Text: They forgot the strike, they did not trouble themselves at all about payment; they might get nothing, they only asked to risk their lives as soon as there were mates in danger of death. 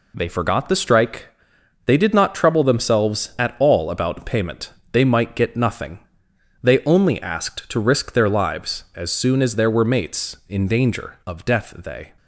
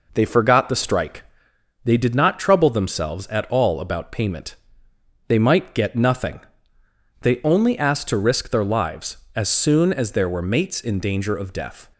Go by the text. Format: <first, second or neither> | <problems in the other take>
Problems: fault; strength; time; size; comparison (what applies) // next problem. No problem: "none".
second | goes on to say "They"; slight; from 11.7 s on; 0.38 s long